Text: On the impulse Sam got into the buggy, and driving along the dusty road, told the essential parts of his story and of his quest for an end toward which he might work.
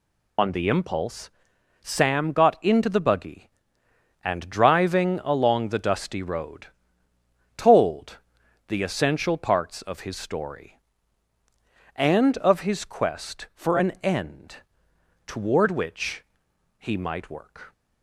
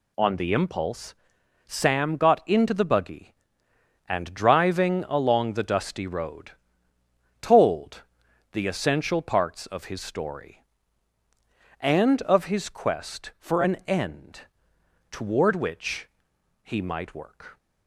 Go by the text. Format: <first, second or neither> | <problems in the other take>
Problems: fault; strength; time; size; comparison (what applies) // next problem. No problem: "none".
second | loses the start of "On"; at 0.3 s; 65 ms // pauses between "impulse" and "Sam"; noticeable; at 1.2 s; 0.52 s long; noticeable in the second // pauses between "told" and "the"; noticeable; at 8.1 s; 0.50 s long; noticeable in the second // pauses between "end" and "toward"; noticeable; at 14.5 s; 0.68 s long; noticeable in the second // pauses between "which" and "he"; noticeable; at 16.2 s; 0.56 s long; noticeable in the second